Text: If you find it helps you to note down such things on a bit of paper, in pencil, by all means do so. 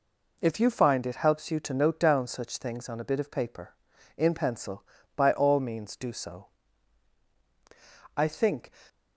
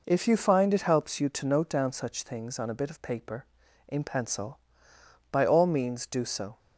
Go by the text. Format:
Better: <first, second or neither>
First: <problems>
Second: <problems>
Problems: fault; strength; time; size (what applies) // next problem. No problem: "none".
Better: second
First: goes on to say "I think"; from 8.1 s on; 0.54 s long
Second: none